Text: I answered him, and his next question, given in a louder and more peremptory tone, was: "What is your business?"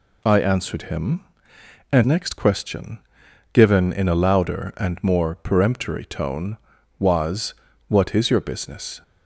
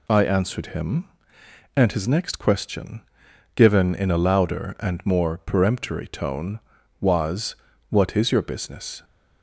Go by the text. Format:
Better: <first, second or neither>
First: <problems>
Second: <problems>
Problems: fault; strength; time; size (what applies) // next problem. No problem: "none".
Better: second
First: skips "his"; at 2.0 s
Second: none